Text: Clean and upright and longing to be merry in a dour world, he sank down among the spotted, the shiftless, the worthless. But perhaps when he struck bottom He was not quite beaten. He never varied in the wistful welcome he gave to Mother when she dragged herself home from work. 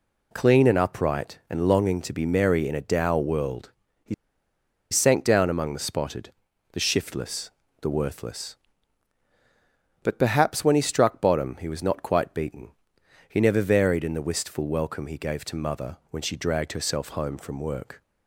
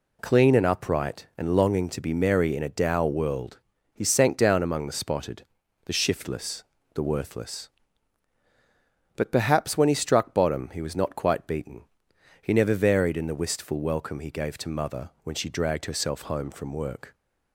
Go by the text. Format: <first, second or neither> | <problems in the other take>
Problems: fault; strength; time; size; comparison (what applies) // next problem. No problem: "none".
second | pauses between "he" and "sank"; noticeable; at 4.1 s; 0.77 s long